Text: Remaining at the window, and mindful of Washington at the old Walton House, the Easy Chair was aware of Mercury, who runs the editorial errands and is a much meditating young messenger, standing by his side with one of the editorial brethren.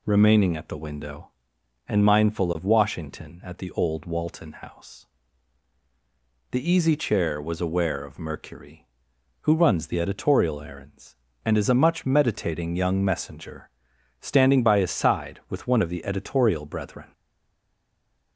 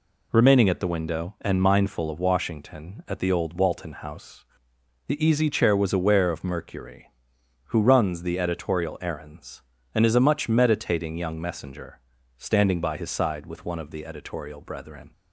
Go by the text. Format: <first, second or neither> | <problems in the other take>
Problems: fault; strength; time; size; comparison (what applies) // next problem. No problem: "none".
second | stays silent after the last word; noticeable; from 17.1 s on; 1.2 s long